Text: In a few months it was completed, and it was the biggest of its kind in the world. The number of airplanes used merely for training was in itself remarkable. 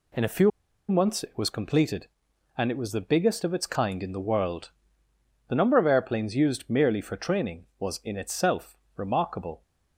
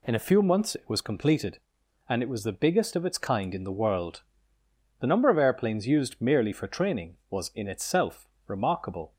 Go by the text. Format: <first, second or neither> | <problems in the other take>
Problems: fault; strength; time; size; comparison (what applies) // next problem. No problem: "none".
second | pauses between "few" and "months"; at 0.5 s; 0.39 s long // pauses between "itself" and "remarkable"; slight; at 8.7 s; 0.22 s long; slight in the second